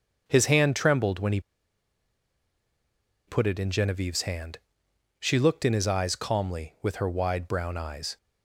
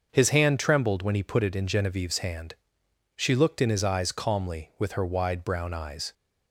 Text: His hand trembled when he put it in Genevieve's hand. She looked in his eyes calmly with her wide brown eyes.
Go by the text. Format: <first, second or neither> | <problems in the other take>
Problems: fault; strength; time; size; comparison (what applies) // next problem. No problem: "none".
second | starts louder than the rest; until 1.2 s; 6.5 dB; also in the second // pauses between "he" and "put"; strong; at 1.3 s; 1.8 s long